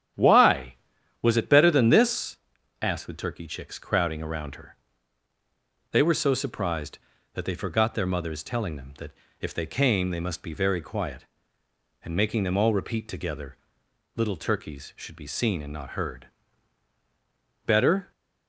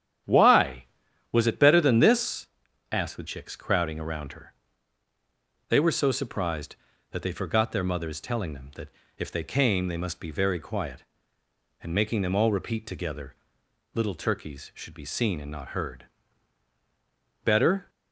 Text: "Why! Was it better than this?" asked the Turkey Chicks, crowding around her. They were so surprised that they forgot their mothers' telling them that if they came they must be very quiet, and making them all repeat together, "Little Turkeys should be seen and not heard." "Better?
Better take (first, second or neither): first